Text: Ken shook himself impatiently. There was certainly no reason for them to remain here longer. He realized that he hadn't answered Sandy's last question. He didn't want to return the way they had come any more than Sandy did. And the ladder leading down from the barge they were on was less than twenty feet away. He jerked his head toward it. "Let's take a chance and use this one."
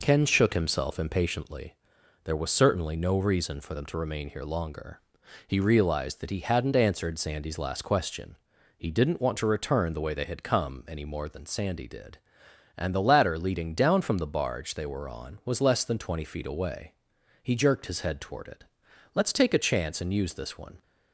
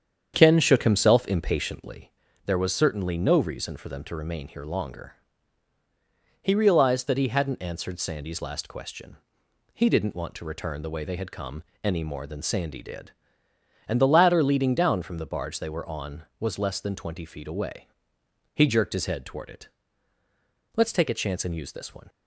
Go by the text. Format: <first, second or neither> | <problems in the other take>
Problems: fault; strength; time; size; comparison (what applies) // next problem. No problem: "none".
first | starts louder than the rest; strong; until 2.3 s; 8 dB // pauses between "come" and "any"; slight; at 11.6 s; 0.20 s long